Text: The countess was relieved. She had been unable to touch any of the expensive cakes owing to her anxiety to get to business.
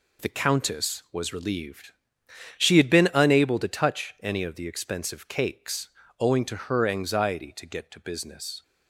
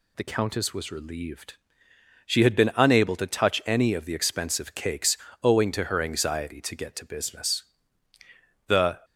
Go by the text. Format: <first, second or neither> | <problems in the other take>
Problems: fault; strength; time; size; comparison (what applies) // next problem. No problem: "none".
first | pauses between "cakes" and "owing"; slight; at 5.1 s; 0.26 s long; slight in the first // goes on to say "The"; slight; from 8.6 s on; 0.36 s long